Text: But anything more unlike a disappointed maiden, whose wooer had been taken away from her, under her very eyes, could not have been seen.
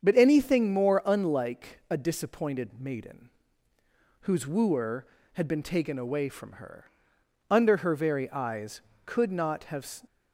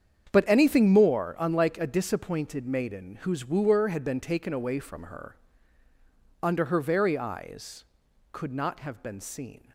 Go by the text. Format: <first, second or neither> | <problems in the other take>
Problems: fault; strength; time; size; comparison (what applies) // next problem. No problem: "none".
second | starts louder than the rest; strong; until 1.0 s; 7.5 dB; strong in the second // stops before "been seen"; at 10.0 s